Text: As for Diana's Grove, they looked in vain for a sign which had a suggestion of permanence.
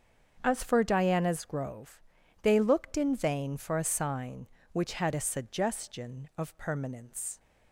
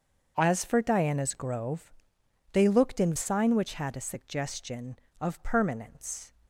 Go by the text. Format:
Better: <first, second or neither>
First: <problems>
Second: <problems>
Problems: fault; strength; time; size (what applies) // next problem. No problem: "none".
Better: first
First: starts louder than the rest; until 1.4 s; 7 dB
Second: starts louder than the rest; until 1.3 s; 6.5 dB // skips "vain for a"; at 3.1 s